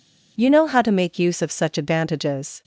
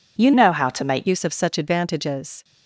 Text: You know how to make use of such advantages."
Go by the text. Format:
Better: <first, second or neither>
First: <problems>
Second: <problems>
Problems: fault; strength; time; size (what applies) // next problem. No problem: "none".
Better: first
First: none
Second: changes voice from "know" to "make"; from 0.3 to 1.0 s; 0.7 s long